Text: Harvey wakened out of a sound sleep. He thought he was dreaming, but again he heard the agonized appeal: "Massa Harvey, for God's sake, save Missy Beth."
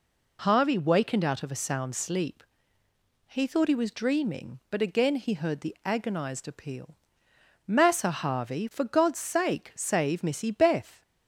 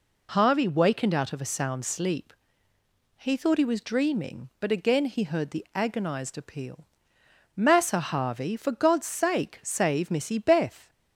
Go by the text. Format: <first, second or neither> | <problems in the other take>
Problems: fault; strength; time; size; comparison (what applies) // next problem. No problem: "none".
neither | none